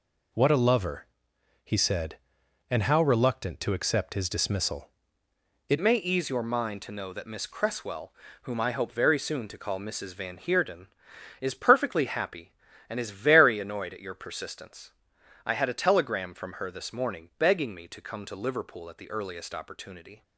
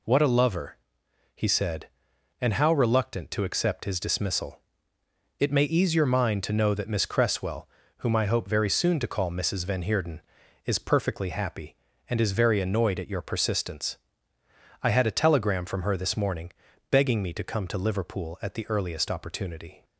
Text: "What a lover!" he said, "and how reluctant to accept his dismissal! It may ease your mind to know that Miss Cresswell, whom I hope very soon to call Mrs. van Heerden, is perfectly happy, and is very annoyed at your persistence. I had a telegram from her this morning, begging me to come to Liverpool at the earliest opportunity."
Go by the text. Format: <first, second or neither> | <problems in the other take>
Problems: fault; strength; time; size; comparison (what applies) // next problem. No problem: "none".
second | changes voice at "may"; from 5.8 s on; 14.4 s long